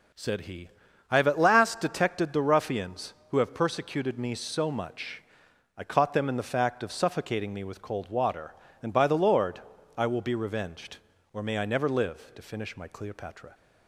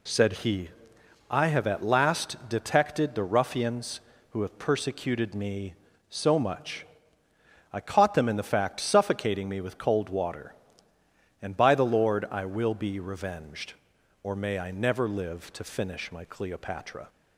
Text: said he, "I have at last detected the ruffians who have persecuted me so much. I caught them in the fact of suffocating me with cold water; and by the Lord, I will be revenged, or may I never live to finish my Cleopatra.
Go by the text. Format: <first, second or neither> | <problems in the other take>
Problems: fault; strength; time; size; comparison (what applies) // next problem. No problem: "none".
first | skips "of"; at 8.8 s